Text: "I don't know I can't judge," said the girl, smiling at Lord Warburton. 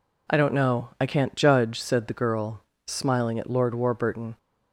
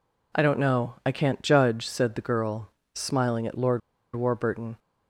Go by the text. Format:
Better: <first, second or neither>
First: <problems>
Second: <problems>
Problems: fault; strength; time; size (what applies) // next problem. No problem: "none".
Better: first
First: none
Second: pauses between "Lord" and "Warburton"; at 3.8 s; 0.36 s long